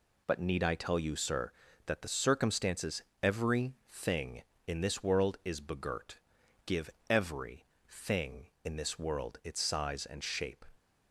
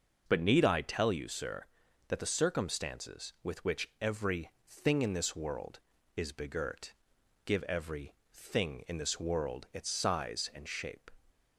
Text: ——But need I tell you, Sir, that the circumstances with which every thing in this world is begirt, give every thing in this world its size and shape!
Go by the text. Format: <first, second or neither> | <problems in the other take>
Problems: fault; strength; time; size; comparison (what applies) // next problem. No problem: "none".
second | skips "with which"; at 3.1 s // pauses between "every" and "thing"; slight; at 3.7 s; 0.16 s long; slight in the second // pauses between "give" and "every"; slight; at 6.8 s; 0.20 s long // pauses between "every" and "thing"; slight; at 7.6 s; 0.26 s long; slight in the second